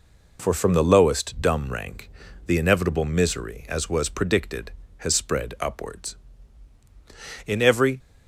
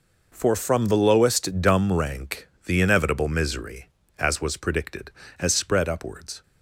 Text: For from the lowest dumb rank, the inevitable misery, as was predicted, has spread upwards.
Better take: second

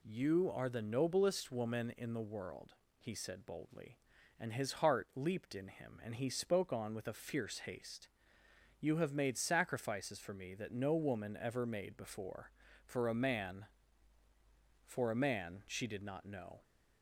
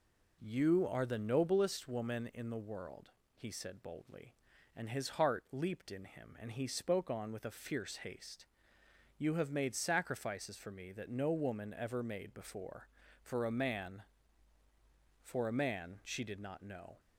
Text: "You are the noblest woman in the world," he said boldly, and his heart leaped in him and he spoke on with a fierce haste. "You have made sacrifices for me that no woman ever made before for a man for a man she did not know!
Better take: first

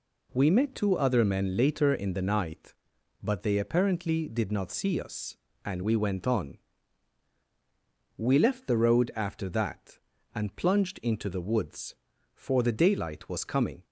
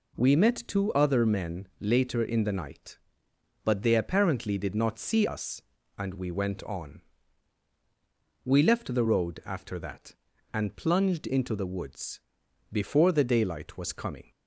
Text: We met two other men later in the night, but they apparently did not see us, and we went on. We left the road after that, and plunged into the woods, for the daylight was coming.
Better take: first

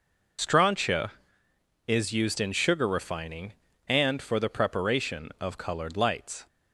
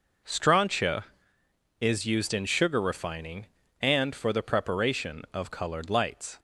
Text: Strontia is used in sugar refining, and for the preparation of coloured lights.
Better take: second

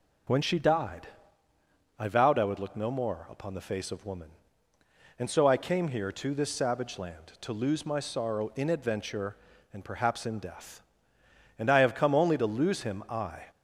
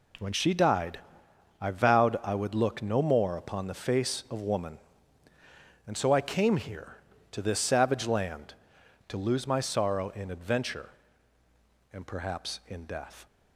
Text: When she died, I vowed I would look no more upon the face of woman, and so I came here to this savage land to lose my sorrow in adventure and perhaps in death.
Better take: second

